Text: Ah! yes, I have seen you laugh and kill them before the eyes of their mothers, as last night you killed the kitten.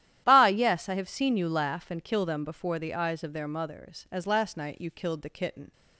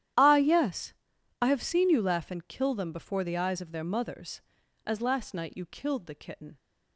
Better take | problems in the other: neither | starts louder than the rest; strong; the same in both

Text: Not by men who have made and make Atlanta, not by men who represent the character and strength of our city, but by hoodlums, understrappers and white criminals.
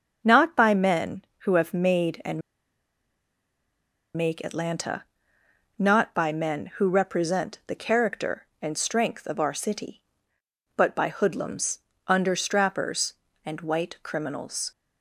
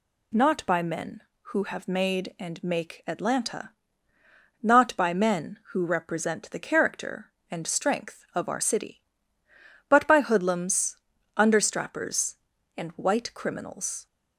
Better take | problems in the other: second | starts louder than the rest; until 1.2 s; 6.5 dB // pauses between "and" and "make"; strong; at 2.4 s; 1.7 s long

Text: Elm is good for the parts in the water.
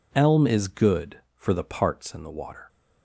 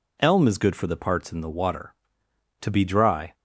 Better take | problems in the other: first | goes on to say "To be dry"; noticeable; from 2.6 s on; 0.72 s long

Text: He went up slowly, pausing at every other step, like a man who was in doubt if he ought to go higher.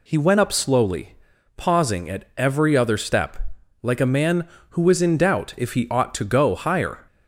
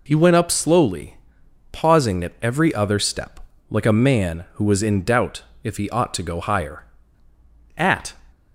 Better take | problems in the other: first | pauses between "doubt" and "if"; slight; at 5.4 s; 0.22 s long // goes on to say "At"; slight; from 7.7 s on; 0.44 s long

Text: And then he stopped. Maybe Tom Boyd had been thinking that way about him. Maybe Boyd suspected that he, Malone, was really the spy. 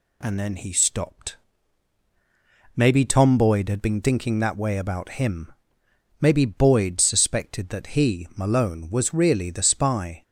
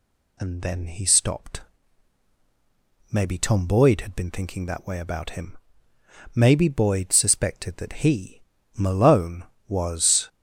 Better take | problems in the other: first | stops before "really the spy"; at 10.2 s

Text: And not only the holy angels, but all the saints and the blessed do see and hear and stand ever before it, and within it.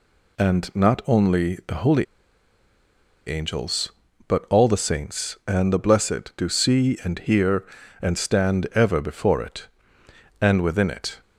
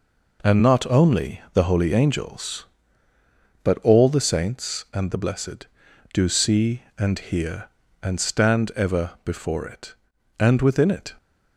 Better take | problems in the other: second | pauses between "holy" and "angels"; at 2.0 s; 1.2 s long

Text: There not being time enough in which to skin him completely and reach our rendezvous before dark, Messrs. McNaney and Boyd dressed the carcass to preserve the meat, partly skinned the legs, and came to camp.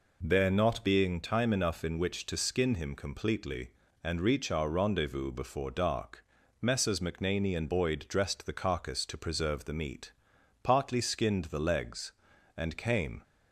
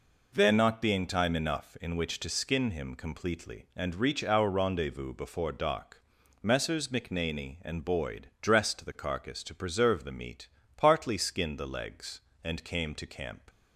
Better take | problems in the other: second | stops before "to camp"; at 13.2 s

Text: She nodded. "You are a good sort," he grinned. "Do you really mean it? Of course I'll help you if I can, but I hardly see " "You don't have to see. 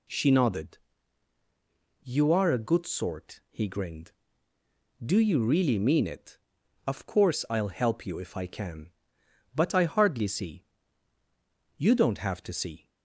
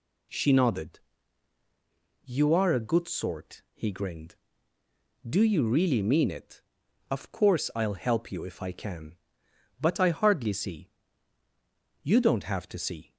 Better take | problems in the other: neither | none

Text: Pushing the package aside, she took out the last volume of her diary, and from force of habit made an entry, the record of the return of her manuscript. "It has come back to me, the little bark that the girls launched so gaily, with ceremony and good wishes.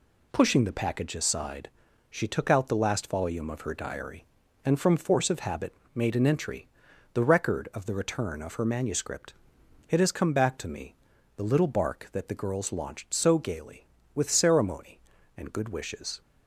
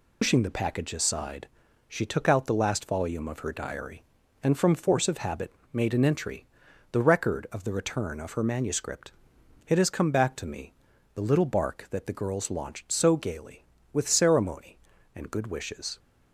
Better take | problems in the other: first | loses the start of "Pushing"; at 0.2 s; 110 ms // pauses between "habit" and "made"; slight; at 5.5 s; 0.20 s long; slight in the first

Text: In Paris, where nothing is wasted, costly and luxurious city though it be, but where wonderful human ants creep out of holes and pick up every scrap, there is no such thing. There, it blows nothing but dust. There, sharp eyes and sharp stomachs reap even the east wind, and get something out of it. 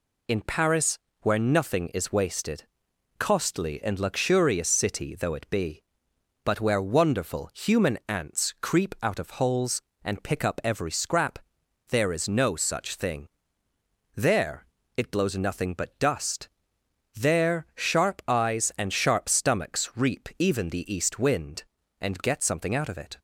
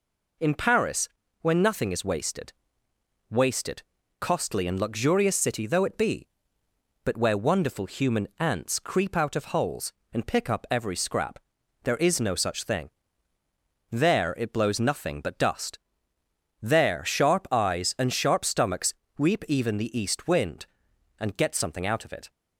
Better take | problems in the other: first | says "wasted" twice; at 3.2 s // pauses between "stomachs" and "reap"; slight; at 18.9 s; 0.24 s long

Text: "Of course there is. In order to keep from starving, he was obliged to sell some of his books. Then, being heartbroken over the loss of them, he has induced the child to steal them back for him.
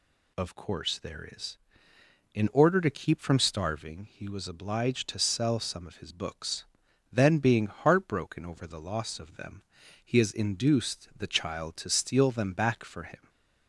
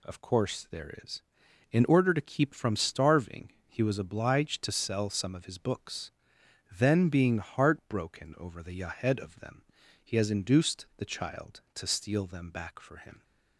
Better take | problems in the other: first | says "yahed" for "loss"; at 8.7 s

